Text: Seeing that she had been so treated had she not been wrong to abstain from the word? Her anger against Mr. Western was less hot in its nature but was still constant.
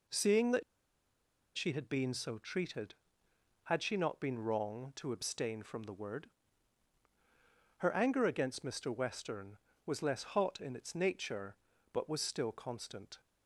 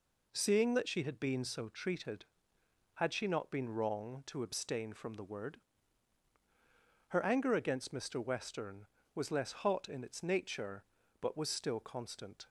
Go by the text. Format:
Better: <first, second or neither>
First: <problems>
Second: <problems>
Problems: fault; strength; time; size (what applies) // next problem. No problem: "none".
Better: second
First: pauses between "that" and "she"; noticeable; at 0.6 s; 0.94 s long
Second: none